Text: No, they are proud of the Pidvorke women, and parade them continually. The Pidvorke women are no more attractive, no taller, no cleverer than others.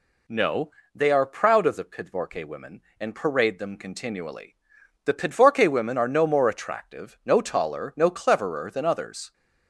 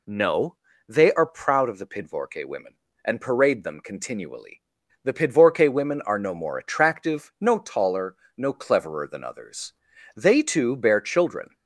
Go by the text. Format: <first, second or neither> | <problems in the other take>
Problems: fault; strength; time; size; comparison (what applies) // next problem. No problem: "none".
first | goes on to say "They too bear children"; from 10.1 s on; 1.3 s long